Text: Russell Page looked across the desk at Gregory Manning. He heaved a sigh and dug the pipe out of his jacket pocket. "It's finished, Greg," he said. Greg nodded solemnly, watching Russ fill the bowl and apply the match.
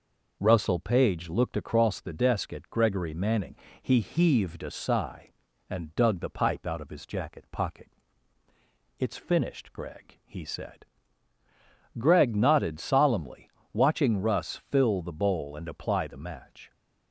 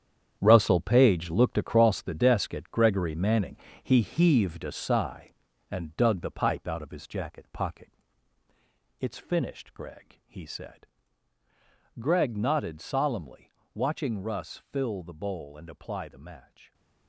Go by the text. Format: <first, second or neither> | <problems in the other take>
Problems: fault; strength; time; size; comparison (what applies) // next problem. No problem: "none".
first | gets quieter; strong; throughout; 11 dB